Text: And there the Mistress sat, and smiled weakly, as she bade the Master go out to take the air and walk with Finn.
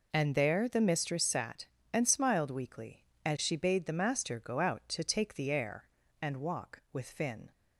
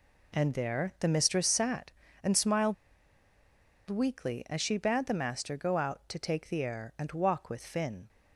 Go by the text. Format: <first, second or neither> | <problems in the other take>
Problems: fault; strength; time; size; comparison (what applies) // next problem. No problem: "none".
first | pauses between "smiled" and "weakly"; at 2.7 s; 1.1 s long